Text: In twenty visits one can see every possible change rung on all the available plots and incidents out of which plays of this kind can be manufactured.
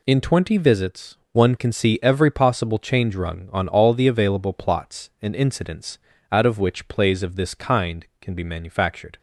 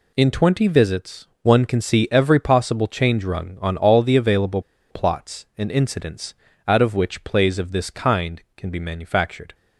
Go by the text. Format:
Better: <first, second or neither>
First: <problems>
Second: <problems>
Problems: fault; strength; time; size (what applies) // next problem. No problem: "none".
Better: first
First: pauses between "visits" and "one"; slight; at 1.1 s; 0.16 s long // pauses between "incidents" and "out"; slight; at 5.9 s; 0.32 s long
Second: pauses between "visits" and "one"; slight; at 1.2 s; 0.16 s long // pauses between "available" and "plots"; slight; at 4.6 s; 0.29 s long // pauses between "incidents" and "out"; slight; at 6.3 s; 0.32 s long